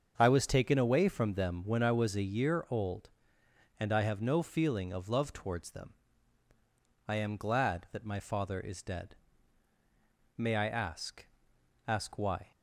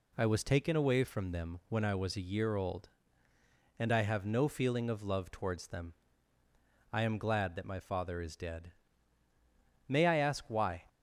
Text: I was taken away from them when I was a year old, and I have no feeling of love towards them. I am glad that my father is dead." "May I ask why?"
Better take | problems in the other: second | starts louder than the rest; until 1.1 s; 7 dB // says "ask" twice; at 11.8 s

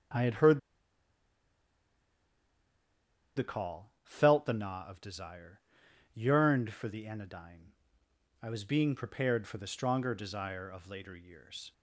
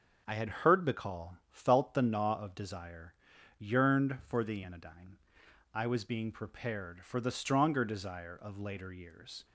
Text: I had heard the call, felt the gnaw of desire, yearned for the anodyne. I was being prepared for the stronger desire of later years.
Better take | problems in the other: second | starts louder than the rest; strong; until 3.9 s; 8 dB; also in the second // pauses between "heard" and "the"; strong; at 0.5 s; 2.7 s long

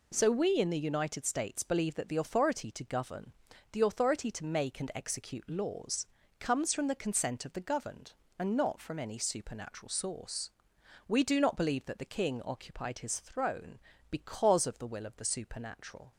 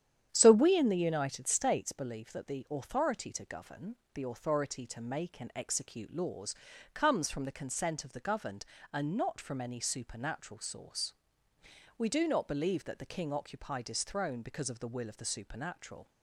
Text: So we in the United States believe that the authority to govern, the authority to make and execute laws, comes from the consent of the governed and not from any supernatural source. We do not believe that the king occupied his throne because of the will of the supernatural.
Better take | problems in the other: first | starts louder than the rest; strong; until 1.9 s; 9.5 dB

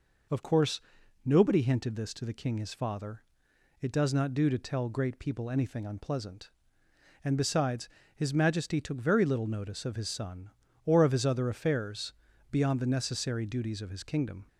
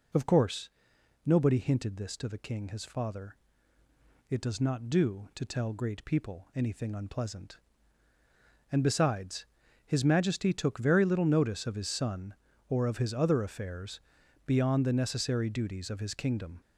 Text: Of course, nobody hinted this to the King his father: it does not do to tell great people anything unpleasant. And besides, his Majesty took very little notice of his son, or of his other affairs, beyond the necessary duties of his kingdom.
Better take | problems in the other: neither | none

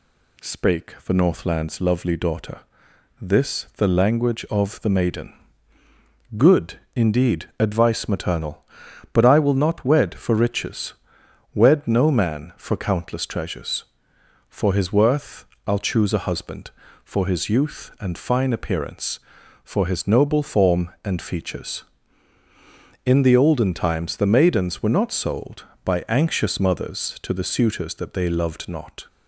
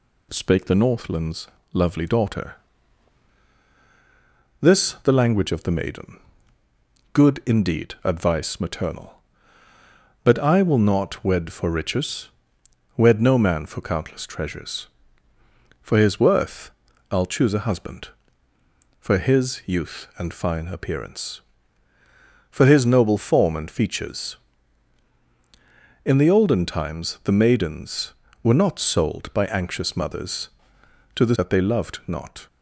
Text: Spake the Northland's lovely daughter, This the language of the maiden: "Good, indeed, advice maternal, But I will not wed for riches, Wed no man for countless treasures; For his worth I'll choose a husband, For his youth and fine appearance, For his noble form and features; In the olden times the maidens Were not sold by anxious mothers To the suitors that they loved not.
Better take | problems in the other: first | pauses between "Northland's" and "lovely"; slight; at 1.4 s; 0.26 s long // pauses between "worth" and "I'll"; at 16.6 s; 0.40 s long; slight in the first // skips "suitors"; at 31.3 s

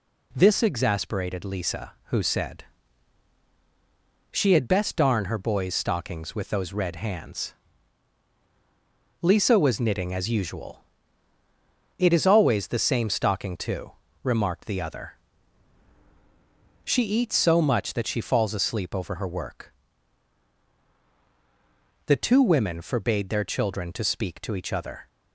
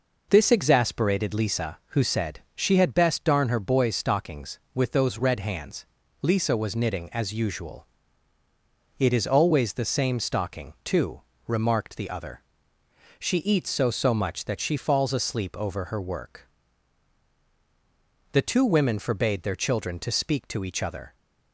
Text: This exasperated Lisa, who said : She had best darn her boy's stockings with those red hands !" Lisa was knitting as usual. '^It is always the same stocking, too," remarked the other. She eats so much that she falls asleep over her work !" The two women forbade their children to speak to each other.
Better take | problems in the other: first | says "so" twice; at 13.8 s

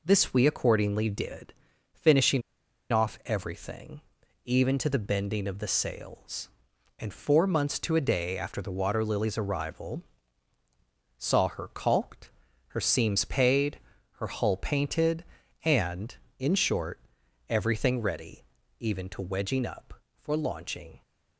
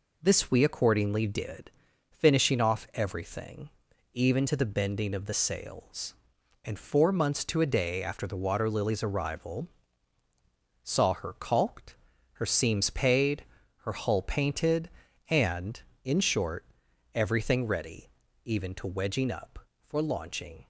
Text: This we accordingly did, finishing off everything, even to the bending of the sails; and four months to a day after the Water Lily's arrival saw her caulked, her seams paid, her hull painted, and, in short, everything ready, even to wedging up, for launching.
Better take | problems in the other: second | pauses between "finishing" and "off"; noticeable; at 2.4 s; 0.50 s long // pauses between "arrival" and "saw"; at 10.0 s; 1.1 s long; also in the second

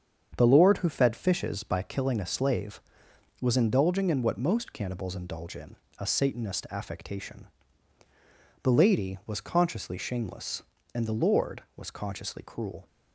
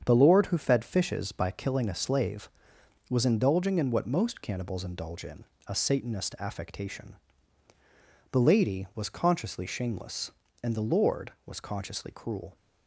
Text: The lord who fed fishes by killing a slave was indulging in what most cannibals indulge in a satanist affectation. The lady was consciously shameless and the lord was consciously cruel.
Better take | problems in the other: neither | starts louder than the rest; strong; the same in both // pauses between "in" and "a"; slight; the same in both

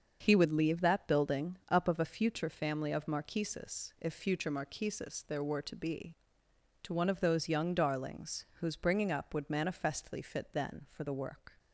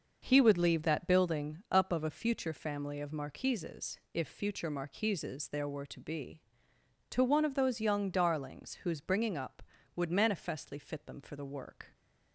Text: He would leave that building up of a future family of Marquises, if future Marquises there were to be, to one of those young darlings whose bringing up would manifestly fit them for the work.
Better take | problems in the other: second | starts louder than the rest; until 1.2 s; 6.5 dB // pauses between "building" and "up"; slight; at 1.5 s; 0.16 s long // says "then" for "them"; at 10.5 s

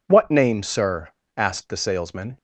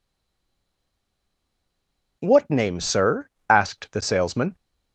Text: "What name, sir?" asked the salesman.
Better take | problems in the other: first | stays silent before the first word; until 2.2 s; 2.2 s long

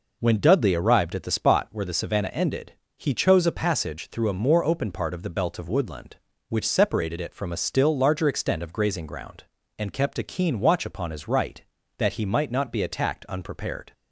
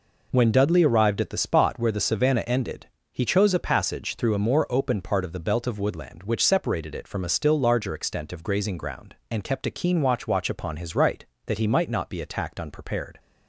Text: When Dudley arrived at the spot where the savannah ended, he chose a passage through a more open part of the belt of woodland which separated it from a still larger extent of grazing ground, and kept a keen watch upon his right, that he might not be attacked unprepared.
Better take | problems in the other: first | says "watch" twice; at 10.2 s

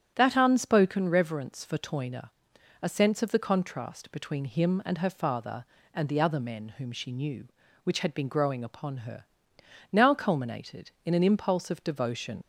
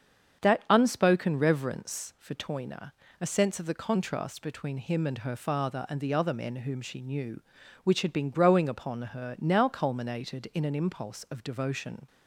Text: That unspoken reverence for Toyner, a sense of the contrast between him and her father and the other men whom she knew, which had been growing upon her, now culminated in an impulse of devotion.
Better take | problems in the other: second | starts louder than the rest; strong; until 1.1 s; 9 dB; strong in the second // leaves "devotion" unfinished; at 12.4 s; 80 ms

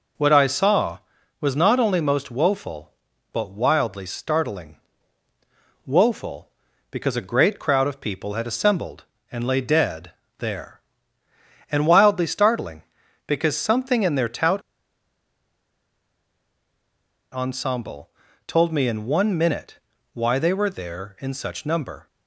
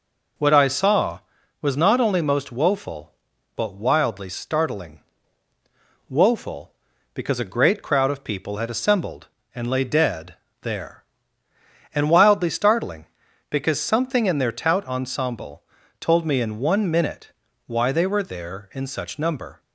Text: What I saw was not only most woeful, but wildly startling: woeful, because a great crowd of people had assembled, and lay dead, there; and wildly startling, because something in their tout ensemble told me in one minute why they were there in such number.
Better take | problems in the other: second | pauses between "tout" and "ensemble"; strong; at 14.6 s; 2.7 s long // pauses between "ensemble" and "told"; at 18.0 s; 0.38 s long; also in the second // pauses between "minute" and "why"; slight; at 19.7 s; 0.34 s long; slight in the second

